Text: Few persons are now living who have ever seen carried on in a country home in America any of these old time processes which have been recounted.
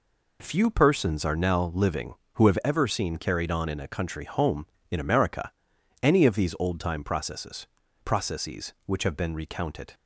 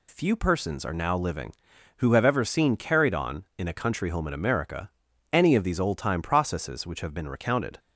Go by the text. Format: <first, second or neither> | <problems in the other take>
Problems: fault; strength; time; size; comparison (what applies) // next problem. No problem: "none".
second | pauses between "America" and "any"; noticeable; at 5.5 s; 0.52 s long; also in the second // says "processes" twice; at 8.0 s